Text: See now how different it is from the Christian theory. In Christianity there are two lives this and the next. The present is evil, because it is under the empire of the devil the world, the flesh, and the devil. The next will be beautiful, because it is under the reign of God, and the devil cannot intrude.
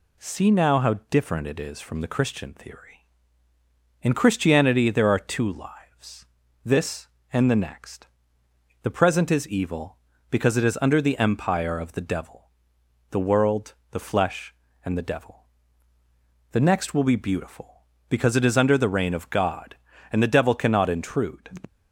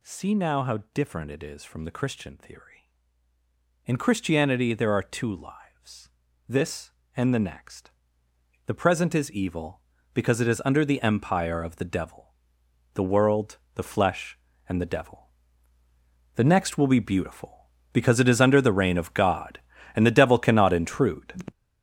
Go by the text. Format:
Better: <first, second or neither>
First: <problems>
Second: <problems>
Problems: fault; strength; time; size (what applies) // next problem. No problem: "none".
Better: first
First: pauses between "how" and "different"; slight; at 0.9 s; 0.16 s long // pauses between "lives" and "this"; at 6.2 s; 0.40 s long // pauses between "devil" and "the"; noticeable; at 12.4 s; 0.64 s long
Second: gets louder; strong; throughout; 8.5 dB // pauses between "how" and "different"; slight; at 0.7 s; 0.16 s long // pauses between "lives" and "this"; at 6.0 s; 0.40 s long // pauses between "devil" and "the"; noticeable; at 12.3 s; 0.64 s long